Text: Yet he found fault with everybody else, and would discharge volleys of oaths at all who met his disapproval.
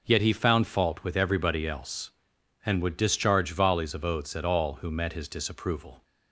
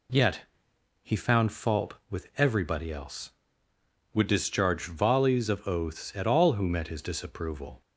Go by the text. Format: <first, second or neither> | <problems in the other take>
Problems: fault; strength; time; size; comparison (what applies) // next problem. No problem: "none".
first | pauses between "Yet" and "he"; noticeable; at 0.4 s; 0.62 s long // skips "and"; at 3.7 s